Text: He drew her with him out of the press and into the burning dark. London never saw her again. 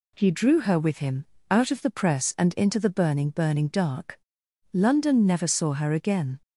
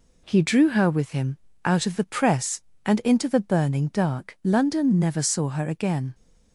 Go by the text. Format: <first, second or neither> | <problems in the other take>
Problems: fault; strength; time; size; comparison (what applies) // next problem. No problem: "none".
second | pauses between "him" and "out"; slight; at 1.2 s; 0.24 s long; slight in the second // says "burning" twice; at 3.2 s